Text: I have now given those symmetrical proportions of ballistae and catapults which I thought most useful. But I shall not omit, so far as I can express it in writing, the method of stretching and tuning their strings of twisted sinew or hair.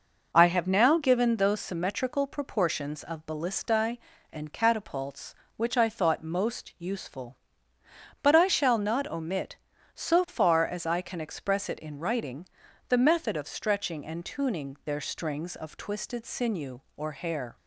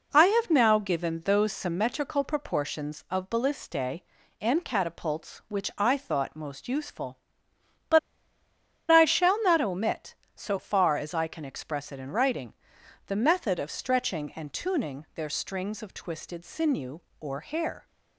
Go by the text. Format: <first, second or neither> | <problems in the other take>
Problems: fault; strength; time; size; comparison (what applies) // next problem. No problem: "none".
first | pauses between "But" and "I"; noticeable; at 7.9 s; 0.92 s long